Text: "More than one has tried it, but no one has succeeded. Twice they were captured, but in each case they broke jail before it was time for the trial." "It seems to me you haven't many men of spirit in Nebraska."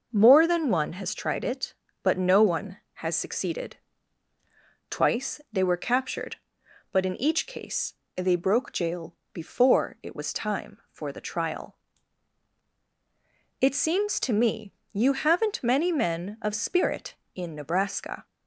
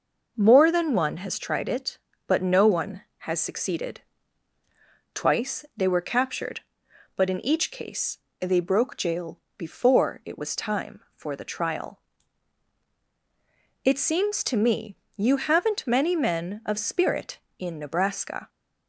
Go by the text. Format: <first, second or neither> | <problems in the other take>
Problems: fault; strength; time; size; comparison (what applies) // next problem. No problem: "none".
neither | pauses between "case" and "they"; slight; the same in both // pauses between "jail" and "before"; slight; the same in both // pauses between "me" and "you"; slight; the same in both